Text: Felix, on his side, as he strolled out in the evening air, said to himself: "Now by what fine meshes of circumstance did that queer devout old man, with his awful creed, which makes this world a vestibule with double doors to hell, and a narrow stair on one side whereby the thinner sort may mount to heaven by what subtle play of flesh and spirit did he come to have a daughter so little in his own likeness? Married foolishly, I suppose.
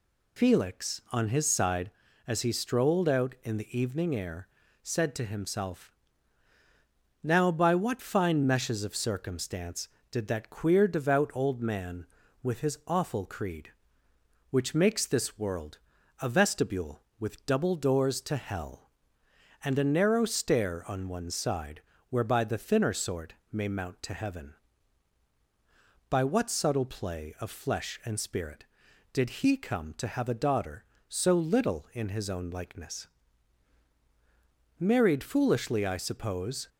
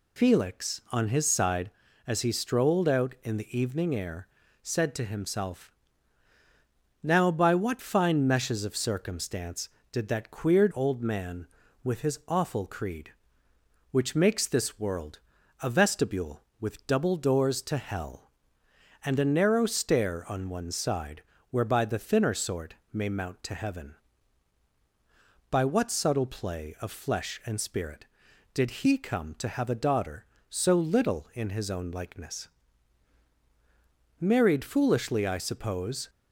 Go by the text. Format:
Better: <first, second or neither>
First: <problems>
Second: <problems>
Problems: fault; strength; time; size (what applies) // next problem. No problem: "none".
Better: first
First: pauses between "world" and "a"; at 15.7 s; 0.42 s long // pauses between "side" and "whereby"; slight; at 21.8 s; 0.30 s long // pauses between "sort" and "may"; slight; at 23.3 s; 0.18 s long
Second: skips "devout"; at 10.7 s // pauses between "world" and "a"; at 15.1 s; 0.42 s long // pauses between "side" and "whereby"; slight; at 21.2 s; 0.30 s long // pauses between "sort" and "may"; slight; at 22.7 s; 0.18 s long